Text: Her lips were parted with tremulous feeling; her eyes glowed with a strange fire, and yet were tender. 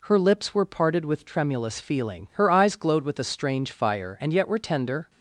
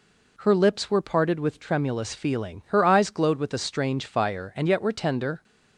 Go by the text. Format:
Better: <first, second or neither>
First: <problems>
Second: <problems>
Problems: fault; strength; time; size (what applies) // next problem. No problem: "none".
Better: neither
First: none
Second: none